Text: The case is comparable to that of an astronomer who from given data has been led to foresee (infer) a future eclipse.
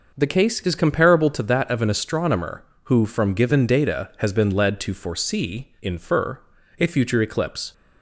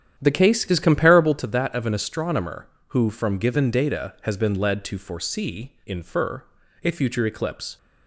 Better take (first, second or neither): first